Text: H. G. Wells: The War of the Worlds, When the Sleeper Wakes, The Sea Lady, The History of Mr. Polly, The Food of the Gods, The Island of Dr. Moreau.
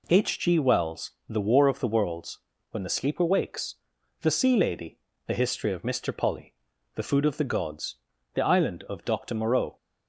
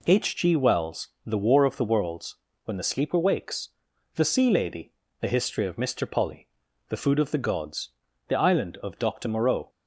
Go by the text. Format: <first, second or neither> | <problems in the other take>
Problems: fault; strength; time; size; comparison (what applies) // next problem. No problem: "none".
neither | none